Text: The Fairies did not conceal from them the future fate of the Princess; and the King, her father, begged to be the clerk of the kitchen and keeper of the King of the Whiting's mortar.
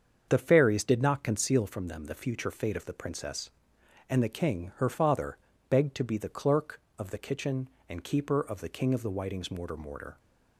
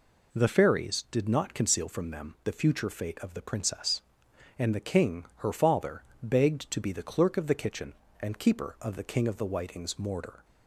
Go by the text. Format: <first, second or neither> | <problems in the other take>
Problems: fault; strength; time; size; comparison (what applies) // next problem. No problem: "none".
second | starts louder than the rest; until 1.3 s; 7 dB // says "mortar" twice; at 9.7 s